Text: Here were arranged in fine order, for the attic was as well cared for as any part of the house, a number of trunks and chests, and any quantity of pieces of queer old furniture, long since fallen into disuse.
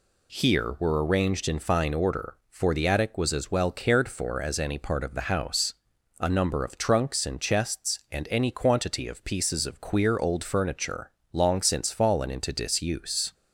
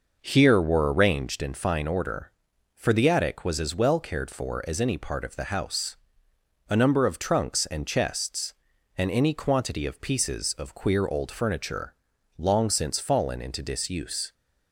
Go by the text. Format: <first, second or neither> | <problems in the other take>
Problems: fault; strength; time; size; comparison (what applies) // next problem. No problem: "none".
first | starts louder than the rest; noticeable; until 1.5 s; 5.5 dB